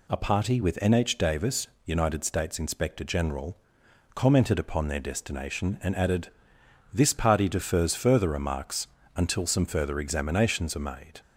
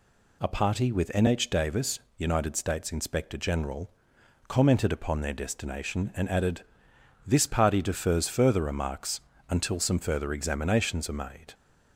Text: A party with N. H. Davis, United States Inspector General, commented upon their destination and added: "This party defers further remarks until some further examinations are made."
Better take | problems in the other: neither | pauses between "remarks" and "until"; slight; the same in both

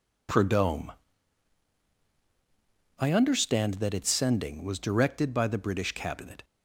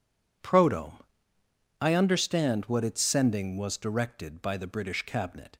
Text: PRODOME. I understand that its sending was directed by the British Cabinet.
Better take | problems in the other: first | says "what" for "that"; at 2.6 s

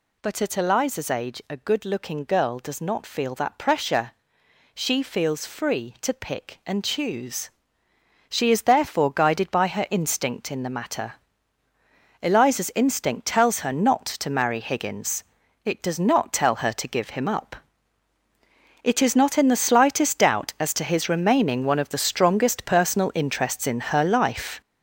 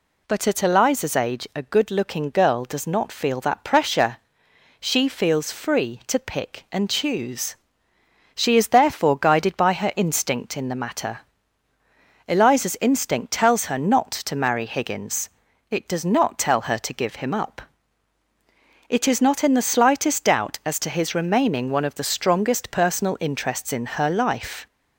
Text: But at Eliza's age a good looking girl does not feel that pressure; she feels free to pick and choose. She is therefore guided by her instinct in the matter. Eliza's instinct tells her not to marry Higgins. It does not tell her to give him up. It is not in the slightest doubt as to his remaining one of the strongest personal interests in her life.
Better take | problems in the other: second | gets louder; strong; throughout; 7.5 dB

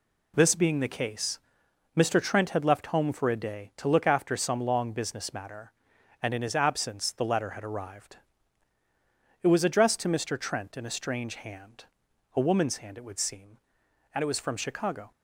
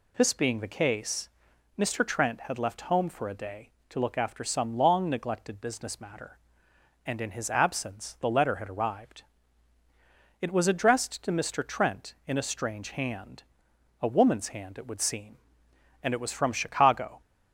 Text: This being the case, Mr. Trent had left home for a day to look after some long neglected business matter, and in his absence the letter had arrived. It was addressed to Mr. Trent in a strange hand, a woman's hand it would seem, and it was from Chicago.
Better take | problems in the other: second | skips "neglected"; at 4.9 s

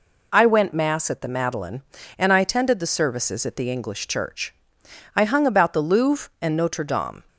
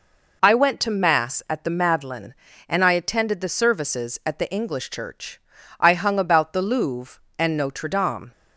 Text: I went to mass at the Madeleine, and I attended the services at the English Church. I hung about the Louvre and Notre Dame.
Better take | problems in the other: second | skips "to"; at 0.7 s

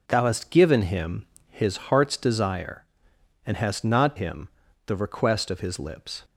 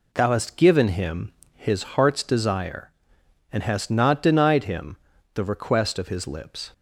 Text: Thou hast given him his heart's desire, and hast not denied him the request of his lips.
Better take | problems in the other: second | pauses between "him" and "his"; slight; at 1.2 s; 0.22 s long; slight in the second // skips "denied"; at 4.1 s // pauses between "him" and "the"; at 4.4 s; 0.38 s long; also in the second

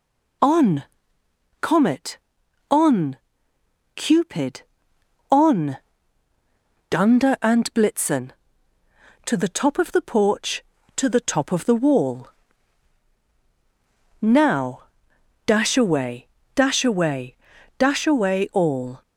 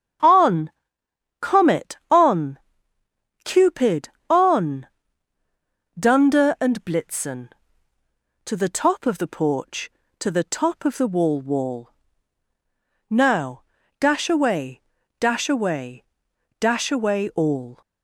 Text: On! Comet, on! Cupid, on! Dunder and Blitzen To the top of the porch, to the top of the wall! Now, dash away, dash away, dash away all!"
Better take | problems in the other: first | starts louder than the rest; strong; until 1.9 s; 8 dB // says "wall" twice; at 11.4 s

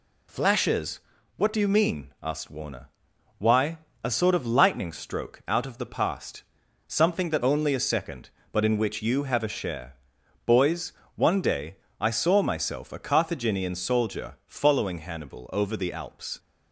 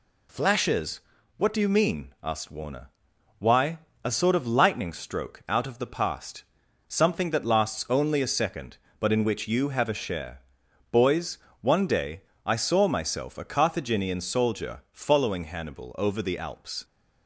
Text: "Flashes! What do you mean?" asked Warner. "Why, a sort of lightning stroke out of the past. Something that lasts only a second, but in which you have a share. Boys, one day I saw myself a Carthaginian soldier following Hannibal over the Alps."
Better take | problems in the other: second | skips "lasts"; at 7.4 s // pauses between "day" and "I"; slight; at 11.7 s; 0.20 s long; slight in the second

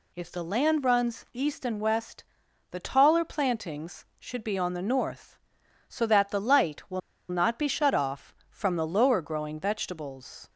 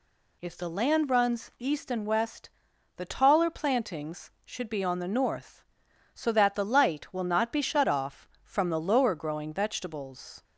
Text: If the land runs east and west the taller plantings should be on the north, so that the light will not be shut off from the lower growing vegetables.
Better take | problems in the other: second | pauses between "west" and "the"; noticeable; at 2.2 s; 0.46 s long; noticeable in the second // pauses between "will" and "not"; slight; at 7.0 s; 0.29 s long

